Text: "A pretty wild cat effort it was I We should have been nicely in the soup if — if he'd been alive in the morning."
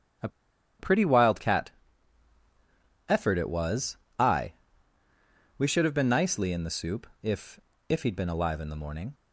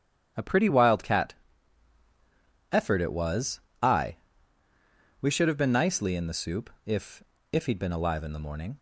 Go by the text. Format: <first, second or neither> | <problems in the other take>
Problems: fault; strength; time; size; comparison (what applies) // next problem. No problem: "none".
second | starts louder than the rest; strong; until 3.1 s; 10.5 dB; strong in the second // pauses between "A" and "pretty"; noticeable; at 0.2 s; 0.51 s long // pauses between "cat" and "effort"; strong; at 1.7 s; 1.3 s long; strong in the second // pauses between "was" and "I"; slight; at 3.9 s; 0.22 s long; slight in the second // pauses between "I" and "We"; at 4.5 s; 1.0 s long; also in the second // pauses between "soup" and "if"; slight; at 7.0 s; 0.16 s long; slight in the second